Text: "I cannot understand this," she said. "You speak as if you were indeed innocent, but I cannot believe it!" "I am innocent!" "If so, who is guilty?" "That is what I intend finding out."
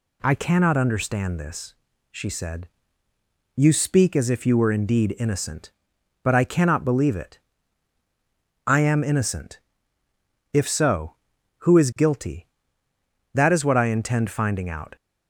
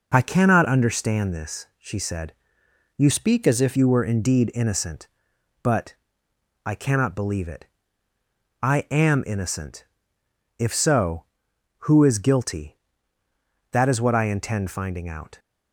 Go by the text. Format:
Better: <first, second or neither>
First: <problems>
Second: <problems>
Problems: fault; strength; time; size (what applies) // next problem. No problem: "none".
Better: first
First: none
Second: changes voice from "speak" to "if"; from 3.1 to 3.7 s; 0.6 s long // pauses between "but" and "I"; noticeable; at 5.9 s; 0.72 s long